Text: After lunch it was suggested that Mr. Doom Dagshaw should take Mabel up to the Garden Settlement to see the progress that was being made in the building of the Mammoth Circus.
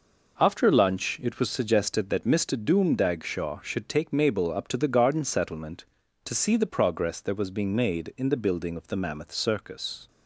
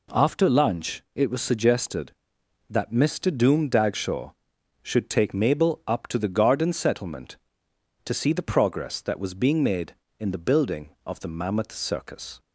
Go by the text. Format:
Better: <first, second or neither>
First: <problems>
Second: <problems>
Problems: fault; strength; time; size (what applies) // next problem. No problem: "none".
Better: neither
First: none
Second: none